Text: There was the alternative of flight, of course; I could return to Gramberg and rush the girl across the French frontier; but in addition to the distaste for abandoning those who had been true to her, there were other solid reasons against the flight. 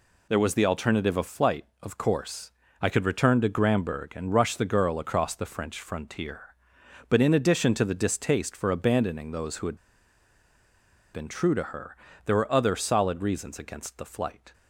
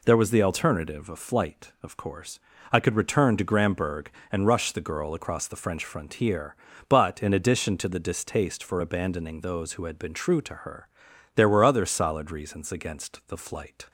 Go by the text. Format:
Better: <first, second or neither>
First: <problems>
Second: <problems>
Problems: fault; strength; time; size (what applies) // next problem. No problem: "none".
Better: second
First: pauses between "had" and "been"; strong; at 9.7 s; 1.3 s long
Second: none